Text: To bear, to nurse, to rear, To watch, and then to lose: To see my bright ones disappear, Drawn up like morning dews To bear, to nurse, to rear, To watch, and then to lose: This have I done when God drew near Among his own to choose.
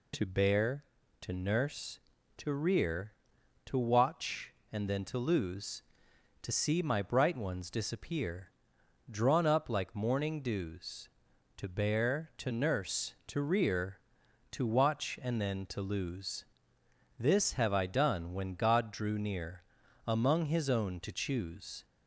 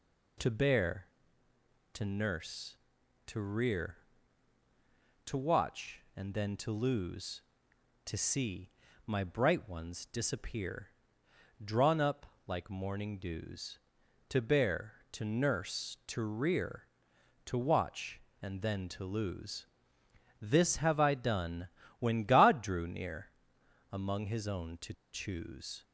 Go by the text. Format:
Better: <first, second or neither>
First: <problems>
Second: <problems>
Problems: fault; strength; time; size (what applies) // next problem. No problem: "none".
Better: first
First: pauses between "near" and "Among"; at 19.6 s; 0.42 s long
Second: pauses between "see" and "my"; slight; at 8.6 s; 0.36 s long // pauses between "up" and "like"; slight; at 12.2 s; 0.22 s long // pauses between "done" and "when"; slight; at 21.6 s; 0.32 s long // pauses between "near" and "Among"; noticeable; at 23.2 s; 0.64 s long // pauses between "to" and "choose"; slight; at 24.9 s; 0.20 s long